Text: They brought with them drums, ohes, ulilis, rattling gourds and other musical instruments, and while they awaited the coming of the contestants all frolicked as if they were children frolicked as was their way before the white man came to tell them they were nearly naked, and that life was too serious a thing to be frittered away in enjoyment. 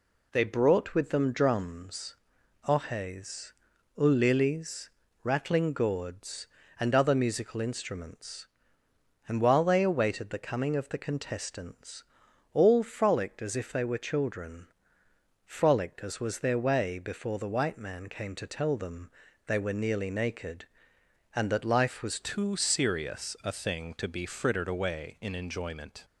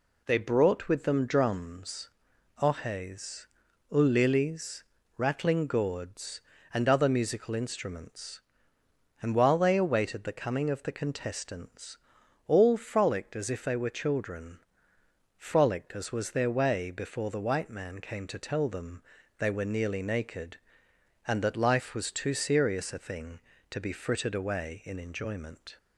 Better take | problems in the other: second | pauses between "contestants" and "all"; noticeable; at 12.0 s; 0.50 s long; noticeable in the second // pauses between "children" and "frolicked"; noticeable; at 14.6 s; 0.78 s long; noticeable in the second // pauses between "them" and "they"; at 19.0 s; 0.38 s long; also in the second // changes voice at "too"; from 22.2 s on; 3.8 s long

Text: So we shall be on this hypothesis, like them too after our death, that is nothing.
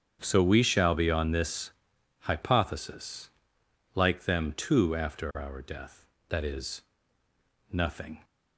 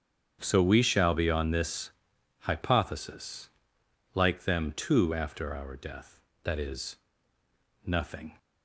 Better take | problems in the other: neither | starts louder than the rest; strong; the same in both // pauses between "this" and "hypothesis"; noticeable; the same in both // pauses between "is" and "nothing"; noticeable; the same in both

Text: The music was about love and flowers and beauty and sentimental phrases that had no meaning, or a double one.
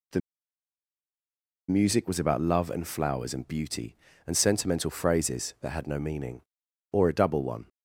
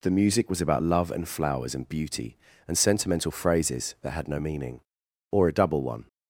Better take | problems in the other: second | pauses between "The" and "music"; strong; at 0.2 s; 1.4 s long

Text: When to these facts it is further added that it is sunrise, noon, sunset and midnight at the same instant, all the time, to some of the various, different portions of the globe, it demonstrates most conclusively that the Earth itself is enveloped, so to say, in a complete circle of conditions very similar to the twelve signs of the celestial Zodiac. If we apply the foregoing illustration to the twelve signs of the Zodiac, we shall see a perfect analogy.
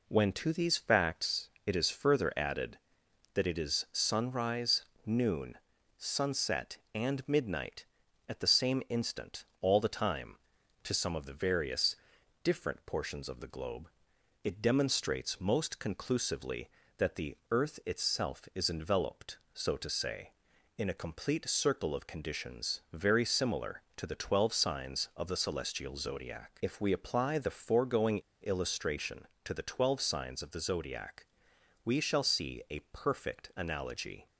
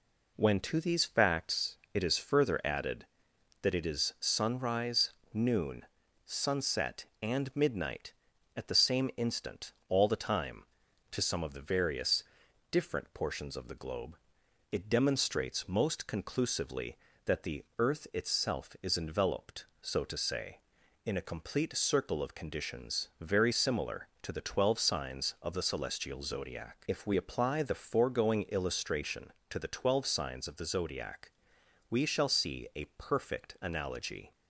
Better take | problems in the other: second | pauses between "facts" and "it"; slight; at 1.4 s; 0.16 s long; slight in the second // pauses between "foregoing" and "illustration"; slight; at 28.1 s; 0.21 s long

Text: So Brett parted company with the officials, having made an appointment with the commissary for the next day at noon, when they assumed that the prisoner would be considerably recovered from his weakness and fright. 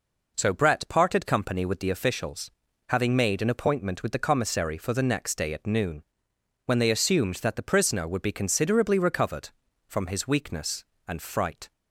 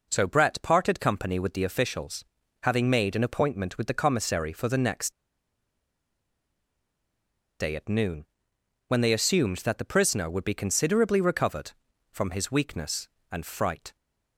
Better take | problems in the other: first | pauses between "next" and "day"; strong; at 5.1 s; 2.4 s long

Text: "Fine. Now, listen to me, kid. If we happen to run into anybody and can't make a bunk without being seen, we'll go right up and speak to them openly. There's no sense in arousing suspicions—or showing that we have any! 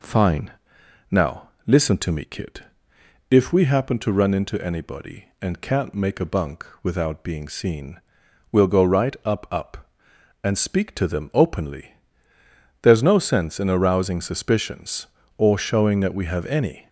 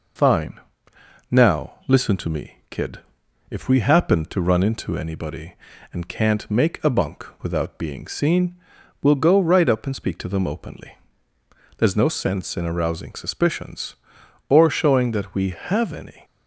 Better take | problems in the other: second | pauses between "bunk" and "without"; slight; at 6.6 s; 0.16 s long; slight in the second // says "up" twice; at 9.5 s

